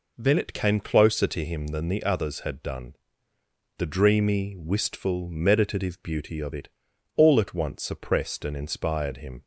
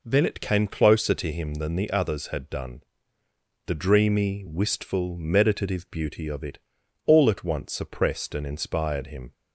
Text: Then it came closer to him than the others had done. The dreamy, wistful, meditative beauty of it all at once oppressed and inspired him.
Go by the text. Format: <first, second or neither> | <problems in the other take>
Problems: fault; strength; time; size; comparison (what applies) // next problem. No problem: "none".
neither | pauses between "it" and "all"; noticeable; the same in both